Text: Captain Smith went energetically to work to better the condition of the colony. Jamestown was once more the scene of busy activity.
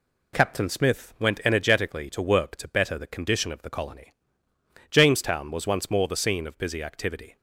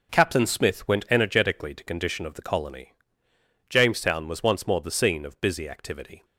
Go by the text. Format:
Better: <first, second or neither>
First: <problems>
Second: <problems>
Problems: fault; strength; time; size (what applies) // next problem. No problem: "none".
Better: first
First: none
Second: skips "work to better the"; at 1.8 s